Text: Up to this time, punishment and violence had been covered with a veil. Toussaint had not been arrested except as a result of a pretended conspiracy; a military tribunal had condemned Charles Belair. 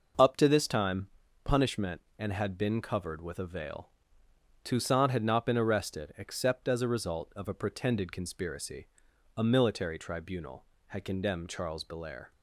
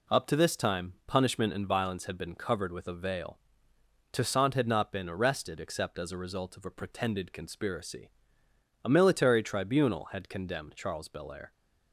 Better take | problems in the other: second | skips "violence"; at 2.3 s

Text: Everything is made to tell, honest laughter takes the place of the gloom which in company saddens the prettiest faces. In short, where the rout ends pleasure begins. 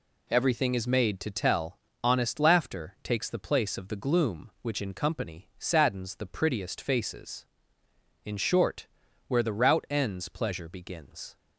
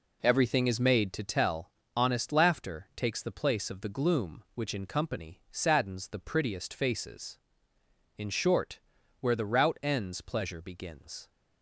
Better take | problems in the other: first | starts louder than the rest; until 1.2 s; 3.5 dB

